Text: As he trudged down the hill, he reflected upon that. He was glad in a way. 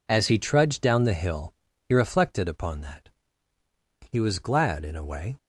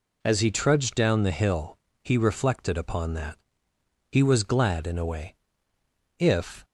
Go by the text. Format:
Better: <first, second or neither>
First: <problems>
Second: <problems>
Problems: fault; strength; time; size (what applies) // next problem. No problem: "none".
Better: first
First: none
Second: goes on to say "If"; slight; from 6.1 s on; 0.46 s long